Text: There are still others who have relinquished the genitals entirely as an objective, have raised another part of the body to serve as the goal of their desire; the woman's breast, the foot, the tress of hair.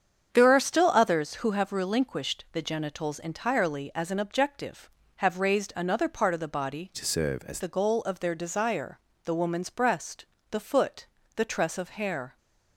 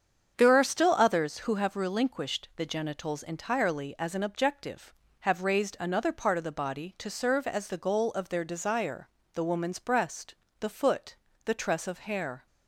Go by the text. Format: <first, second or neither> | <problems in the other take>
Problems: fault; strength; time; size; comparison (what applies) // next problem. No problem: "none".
second | starts louder than the rest; strong; until 1.3 s; 7.5 dB; strong in the second // changes voice from "to" to "as"; from 6.9 to 7.5 s; 0.6 s long